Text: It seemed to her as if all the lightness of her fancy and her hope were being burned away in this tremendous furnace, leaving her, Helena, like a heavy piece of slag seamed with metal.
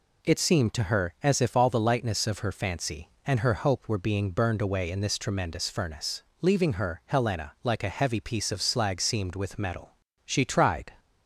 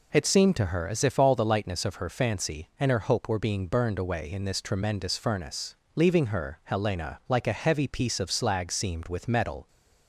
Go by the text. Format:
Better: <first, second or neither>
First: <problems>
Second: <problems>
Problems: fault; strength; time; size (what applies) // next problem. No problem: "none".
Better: second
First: goes on to say "She tried"; noticeable; from 10.2 s on; 0.68 s long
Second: none